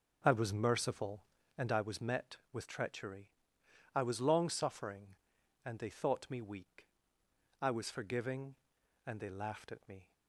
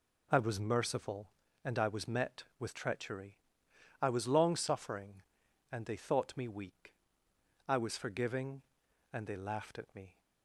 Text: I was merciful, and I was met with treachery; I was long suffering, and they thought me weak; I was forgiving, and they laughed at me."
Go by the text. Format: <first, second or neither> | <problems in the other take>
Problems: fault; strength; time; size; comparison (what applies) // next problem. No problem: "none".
second | starts louder than the rest; until 1.9 s; 6.5 dB